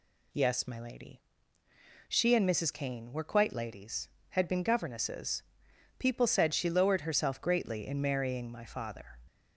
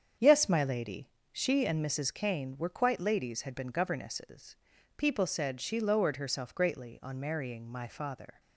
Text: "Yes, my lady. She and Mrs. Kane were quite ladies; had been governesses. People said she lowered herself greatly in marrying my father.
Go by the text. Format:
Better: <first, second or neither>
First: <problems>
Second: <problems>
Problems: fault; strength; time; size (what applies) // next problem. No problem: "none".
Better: first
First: none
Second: starts louder than the rest; strong; until 1.4 s; 7.5 dB // says "on" for "in"; at 7.0 s